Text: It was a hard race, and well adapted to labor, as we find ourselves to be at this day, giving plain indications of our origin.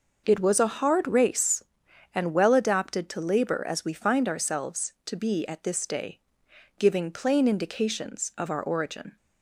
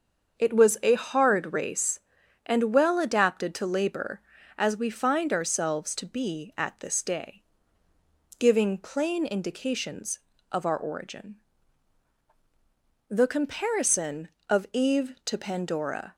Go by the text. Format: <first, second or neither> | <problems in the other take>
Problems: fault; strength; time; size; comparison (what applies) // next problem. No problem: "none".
first | starts louder than the rest; until 1.4 s; 7 dB // goes on to say "The comparison of Eve to Pandora"; strong; from 13.0 s on; 3.0 s long